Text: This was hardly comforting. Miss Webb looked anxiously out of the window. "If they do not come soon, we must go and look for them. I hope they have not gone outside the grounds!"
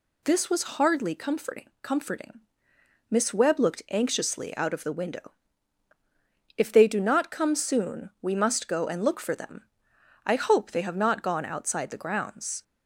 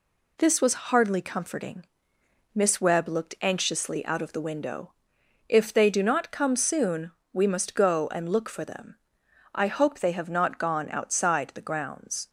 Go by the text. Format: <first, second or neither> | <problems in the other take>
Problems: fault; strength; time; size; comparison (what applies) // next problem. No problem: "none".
second | says "comforting" twice; at 1.8 s